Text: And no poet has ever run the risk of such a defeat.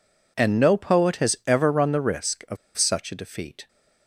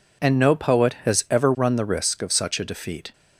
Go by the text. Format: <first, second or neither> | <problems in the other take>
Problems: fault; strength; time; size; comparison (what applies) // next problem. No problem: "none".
second | pauses between "of" and "such"; slight; at 2.5 s; 0.20 s long